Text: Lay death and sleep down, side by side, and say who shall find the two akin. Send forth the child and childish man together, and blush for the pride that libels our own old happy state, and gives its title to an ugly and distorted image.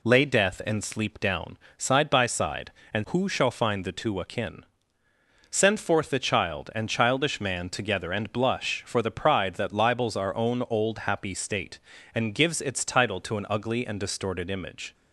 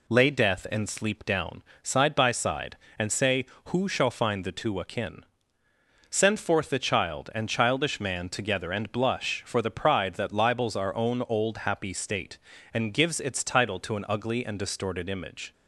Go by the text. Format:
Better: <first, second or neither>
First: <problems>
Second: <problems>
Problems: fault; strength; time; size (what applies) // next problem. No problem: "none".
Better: second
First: skips "say"; at 3.0 s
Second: none